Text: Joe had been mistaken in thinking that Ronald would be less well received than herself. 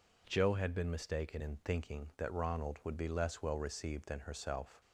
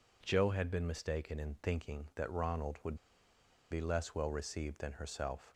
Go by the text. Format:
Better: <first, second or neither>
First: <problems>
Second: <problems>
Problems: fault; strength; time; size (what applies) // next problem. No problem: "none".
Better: first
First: none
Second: pauses between "would" and "be"; noticeable; at 2.9 s; 0.75 s long